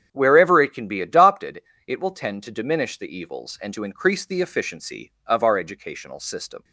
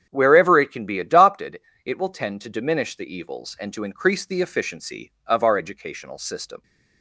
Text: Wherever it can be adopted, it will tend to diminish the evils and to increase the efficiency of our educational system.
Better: neither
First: starts louder than the rest; strong; until 1.1 s; 8.5 dB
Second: starts louder than the rest; strong; until 1.1 s; 8.5 dB

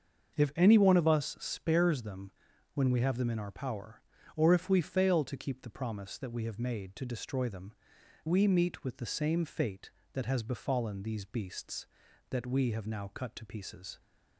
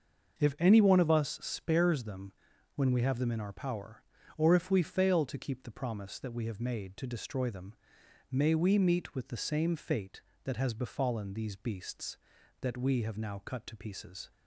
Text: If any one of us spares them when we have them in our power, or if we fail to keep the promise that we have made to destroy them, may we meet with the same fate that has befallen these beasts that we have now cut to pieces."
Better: second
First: starts louder than the rest; until 1.4 s; 6.5 dB // pauses between "them" and "when"; at 2.3 s; 0.42 s long // skips "may"; at 7.9 s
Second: starts louder than the rest; until 1.4 s; 6 dB // pauses between "them" and "when"; at 2.3 s; 0.42 s long

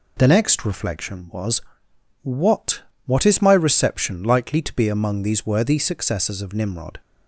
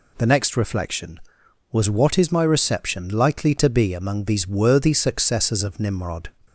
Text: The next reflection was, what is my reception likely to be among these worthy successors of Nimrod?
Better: second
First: says "what" twice; at 3.0 s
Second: none

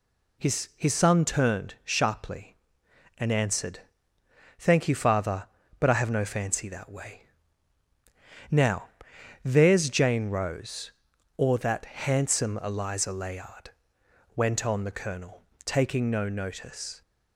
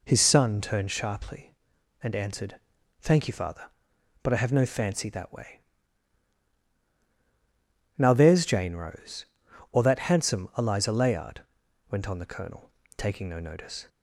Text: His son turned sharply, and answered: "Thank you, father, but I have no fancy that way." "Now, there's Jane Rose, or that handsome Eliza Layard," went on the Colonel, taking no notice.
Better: second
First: says "His" twice; at 0.7 s // pauses between "that" and "handsome"; slight; at 11.8 s; 0.24 s long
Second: none

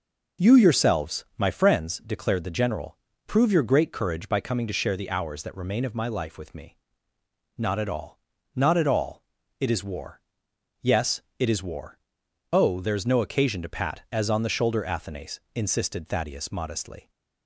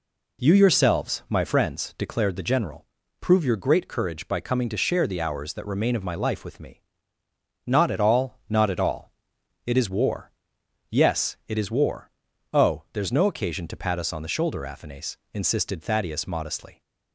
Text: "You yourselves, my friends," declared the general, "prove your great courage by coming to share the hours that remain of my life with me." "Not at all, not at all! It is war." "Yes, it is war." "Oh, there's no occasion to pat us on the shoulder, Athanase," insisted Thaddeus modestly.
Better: second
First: says "as" for "us"; at 14.1 s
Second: none

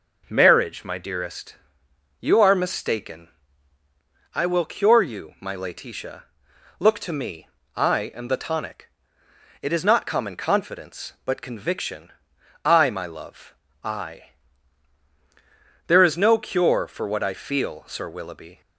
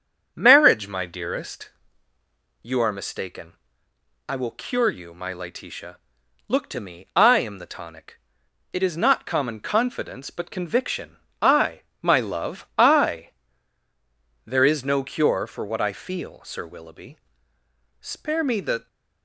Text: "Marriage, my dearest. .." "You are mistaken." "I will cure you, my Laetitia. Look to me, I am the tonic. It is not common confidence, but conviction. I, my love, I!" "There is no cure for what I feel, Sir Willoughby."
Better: first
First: none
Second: starts louder than the rest; strong; until 1.3 s; 7.5 dB // goes on to say "Spare me the"; noticeable; from 18.0 s on; 0.86 s long

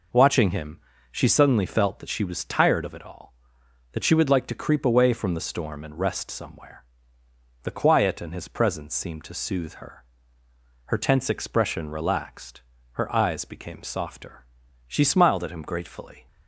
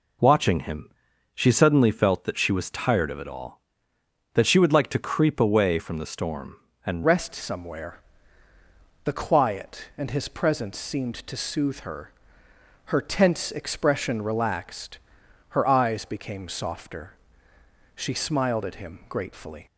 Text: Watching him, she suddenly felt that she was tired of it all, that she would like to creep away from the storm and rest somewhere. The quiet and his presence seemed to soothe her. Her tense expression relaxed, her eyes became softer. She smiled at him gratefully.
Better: first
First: none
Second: changes voice at "rest"; from 7.0 s on; 12.6 s long

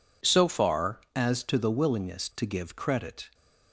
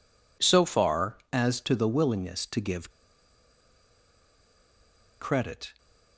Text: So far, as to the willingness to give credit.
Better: first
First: none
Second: pauses between "give" and "credit"; strong; at 2.9 s; 2.2 s long

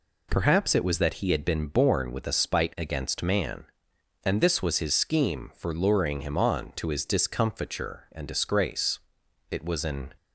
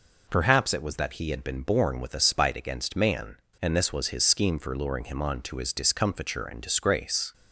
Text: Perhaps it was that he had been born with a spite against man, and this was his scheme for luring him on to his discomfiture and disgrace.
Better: second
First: goes on to say "It was an"; noticeable; from 9.4 s on; 0.64 s long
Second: none

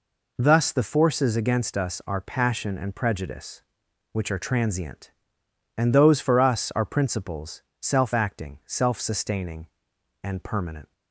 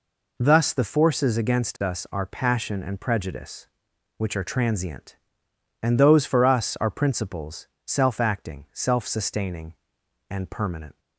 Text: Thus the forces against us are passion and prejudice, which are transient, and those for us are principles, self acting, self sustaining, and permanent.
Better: neither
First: none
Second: none

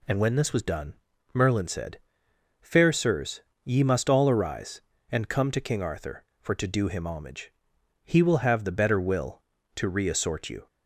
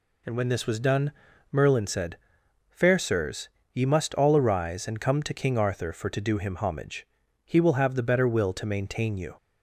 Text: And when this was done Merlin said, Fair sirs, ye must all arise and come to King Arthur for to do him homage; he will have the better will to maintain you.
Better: second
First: pauses between "done" and "Merlin"; at 0.9 s; 0.40 s long // says "reassort" for "maintain"; at 9.8 s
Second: pauses between "done" and "Merlin"; at 1.1 s; 0.40 s long

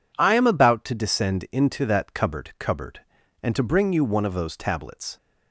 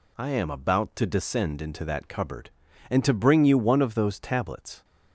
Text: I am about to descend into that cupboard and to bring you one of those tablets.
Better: second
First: says "cupboard" twice; at 2.5 s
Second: none

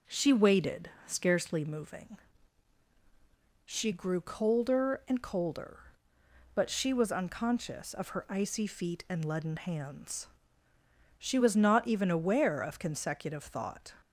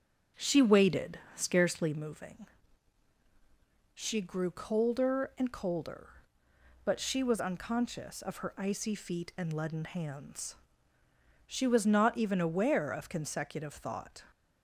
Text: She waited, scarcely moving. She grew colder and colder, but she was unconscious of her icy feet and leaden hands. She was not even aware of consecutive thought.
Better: first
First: none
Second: starts louder than the rest; until 2.0 s; 7 dB

